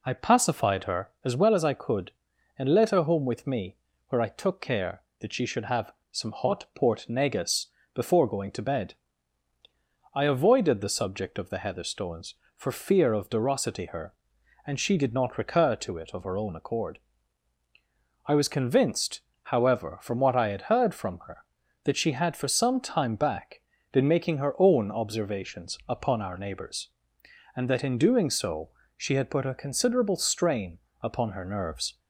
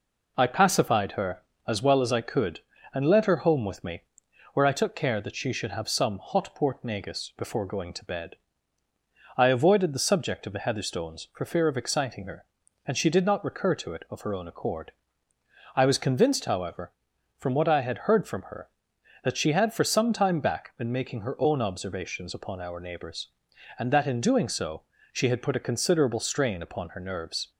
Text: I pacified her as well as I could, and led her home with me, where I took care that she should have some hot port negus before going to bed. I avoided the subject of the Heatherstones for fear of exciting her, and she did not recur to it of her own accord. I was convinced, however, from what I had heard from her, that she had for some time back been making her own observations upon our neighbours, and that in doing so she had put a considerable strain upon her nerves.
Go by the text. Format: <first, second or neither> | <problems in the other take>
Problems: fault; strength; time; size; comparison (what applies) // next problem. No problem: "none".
second | pauses between "have" and "some"; slight; at 5.9 s; 0.20 s long // pauses between "negus" and "before"; slight; at 7.6 s; 0.28 s long // says "derosity" for "exciting"; at 13.2 s // pauses between "back" and "been"; slight; at 23.6 s; 0.30 s long // pauses between "so" and "she"; slight; at 28.6 s; 0.28 s long; slight in the second // pauses between "strain" and "upon"; slight; at 30.7 s; 0.24 s long